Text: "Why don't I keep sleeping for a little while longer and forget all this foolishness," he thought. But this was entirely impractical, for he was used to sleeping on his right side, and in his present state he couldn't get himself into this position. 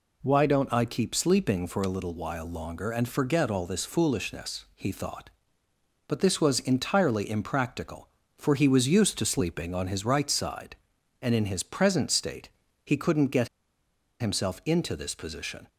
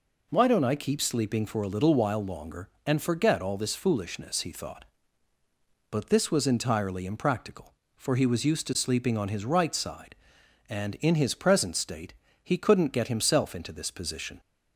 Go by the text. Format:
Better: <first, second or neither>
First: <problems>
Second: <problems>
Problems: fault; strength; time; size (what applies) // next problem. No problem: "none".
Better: second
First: pauses between "state" and "he"; slight; at 12.4 s; 0.34 s long // pauses between "get" and "himself"; noticeable; at 13.4 s; 0.72 s long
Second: pauses between "state" and "he"; slight; at 12.1 s; 0.30 s long